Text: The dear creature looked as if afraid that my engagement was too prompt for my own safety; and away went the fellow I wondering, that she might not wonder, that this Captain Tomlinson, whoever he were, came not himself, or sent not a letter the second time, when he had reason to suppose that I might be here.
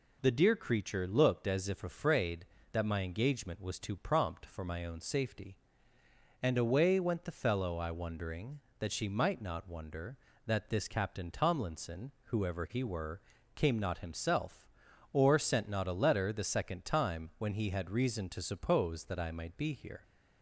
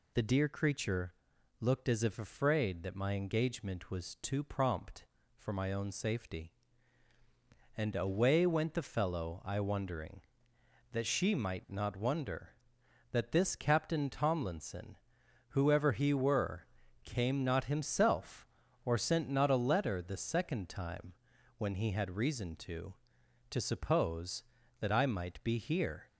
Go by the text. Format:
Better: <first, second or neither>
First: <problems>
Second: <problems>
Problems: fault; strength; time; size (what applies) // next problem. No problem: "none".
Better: first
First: none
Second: pauses between "creature" and "looked"; noticeable; at 1.1 s; 0.46 s long // says "to" twice; at 23.4 s